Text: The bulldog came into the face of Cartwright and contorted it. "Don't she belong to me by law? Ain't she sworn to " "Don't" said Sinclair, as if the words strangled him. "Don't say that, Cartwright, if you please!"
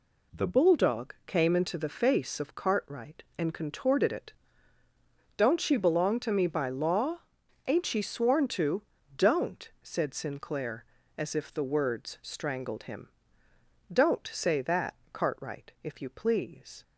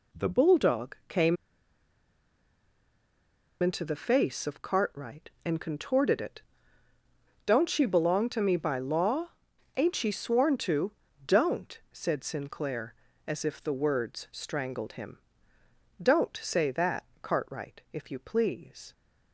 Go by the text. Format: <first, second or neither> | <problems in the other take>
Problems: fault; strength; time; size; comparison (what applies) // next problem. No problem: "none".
first | pauses between "came" and "into"; strong; at 1.3 s; 2.2 s long